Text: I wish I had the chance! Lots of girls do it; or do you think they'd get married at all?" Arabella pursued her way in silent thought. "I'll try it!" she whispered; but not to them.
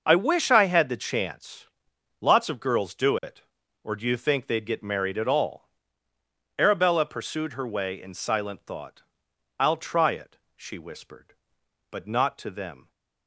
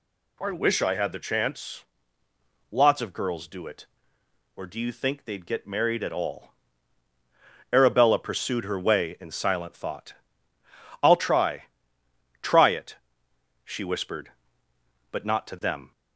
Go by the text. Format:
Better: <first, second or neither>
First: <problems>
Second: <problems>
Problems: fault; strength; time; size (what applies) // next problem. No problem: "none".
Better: first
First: none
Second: says "try" twice; at 12.4 s